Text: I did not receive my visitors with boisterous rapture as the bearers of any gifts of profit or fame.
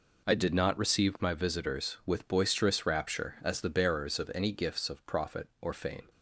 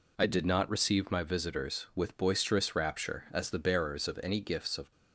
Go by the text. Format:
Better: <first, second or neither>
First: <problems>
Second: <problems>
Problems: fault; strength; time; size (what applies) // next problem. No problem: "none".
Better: first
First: none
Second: stops before "profit or fame"; at 4.9 s